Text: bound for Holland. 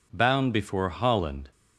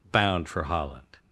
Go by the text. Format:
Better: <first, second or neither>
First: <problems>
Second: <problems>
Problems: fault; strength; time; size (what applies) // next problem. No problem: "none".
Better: second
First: says "before" for "for"; at 0.5 s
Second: none